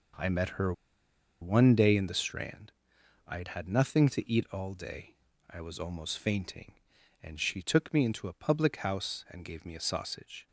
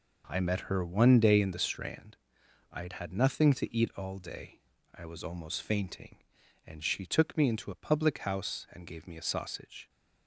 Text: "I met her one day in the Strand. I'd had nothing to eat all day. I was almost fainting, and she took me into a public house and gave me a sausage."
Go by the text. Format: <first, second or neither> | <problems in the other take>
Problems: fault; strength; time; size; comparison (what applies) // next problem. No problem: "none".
second | pauses between "her" and "one"; noticeable; at 0.7 s; 0.68 s long